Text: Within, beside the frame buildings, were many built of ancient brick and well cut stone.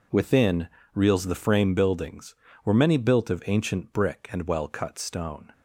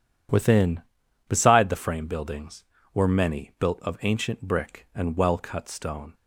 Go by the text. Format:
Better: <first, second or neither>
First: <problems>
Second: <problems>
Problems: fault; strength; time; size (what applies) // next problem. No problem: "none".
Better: second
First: says "reels" for "beside"; at 0.9 s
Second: none